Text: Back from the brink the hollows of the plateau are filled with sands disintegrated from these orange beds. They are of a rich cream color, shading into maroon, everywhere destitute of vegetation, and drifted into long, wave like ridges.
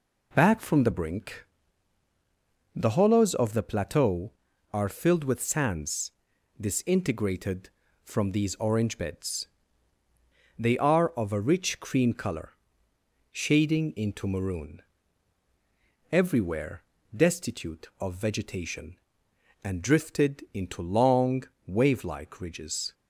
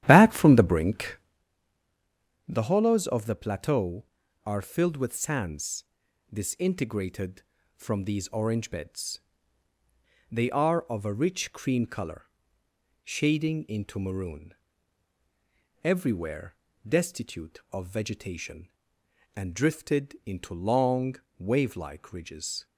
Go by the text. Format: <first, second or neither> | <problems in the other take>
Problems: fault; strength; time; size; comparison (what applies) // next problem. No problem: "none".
first | starts louder than the rest; strong; until 1.4 s; 11.5 dB // pauses between "brink" and "the"; strong; at 1.1 s; 1.3 s long; strong in the first // pauses between "sands" and "disintegrated"; noticeable; at 5.8 s; 0.48 s long; noticeable in the first // pauses between "everywhere" and "destitute"; slight; at 16.5 s; 0.30 s long; slight in the first